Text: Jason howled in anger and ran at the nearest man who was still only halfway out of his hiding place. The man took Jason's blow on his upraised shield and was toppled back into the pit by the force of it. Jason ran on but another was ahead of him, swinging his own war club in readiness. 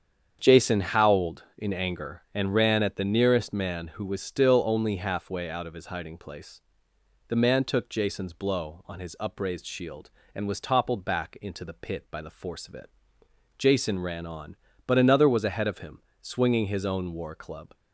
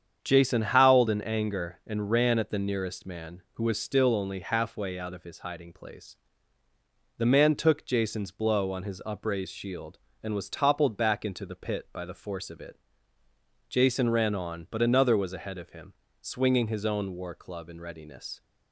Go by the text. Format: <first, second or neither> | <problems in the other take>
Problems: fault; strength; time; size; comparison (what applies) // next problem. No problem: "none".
second | starts louder than the rest; strong; until 1.4 s; 8 dB; strong in the second // stops before "in readiness"; at 17.7 s